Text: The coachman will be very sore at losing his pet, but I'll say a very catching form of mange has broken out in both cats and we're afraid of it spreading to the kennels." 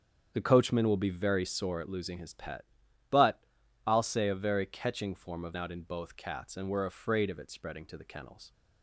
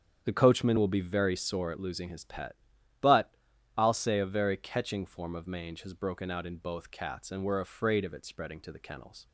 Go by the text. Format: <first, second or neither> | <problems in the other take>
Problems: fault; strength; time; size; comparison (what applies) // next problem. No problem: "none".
second | starts louder than the rest; strong; until 1.3 s; 8 dB; strong in the second // pauses between "but" and "I'll"; noticeable; at 3.3 s; 0.46 s long; noticeable in the second // skips "mange has broken"; at 5.5 s